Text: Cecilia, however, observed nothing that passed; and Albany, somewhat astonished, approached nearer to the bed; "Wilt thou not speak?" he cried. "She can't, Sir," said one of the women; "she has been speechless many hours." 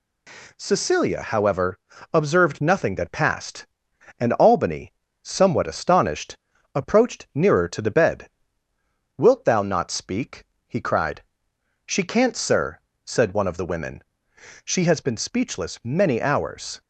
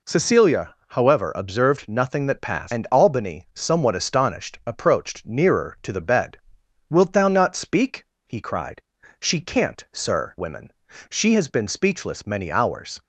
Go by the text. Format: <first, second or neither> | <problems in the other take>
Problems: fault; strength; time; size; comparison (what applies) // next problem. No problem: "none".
first | skips "said one of the"; at 10.3 s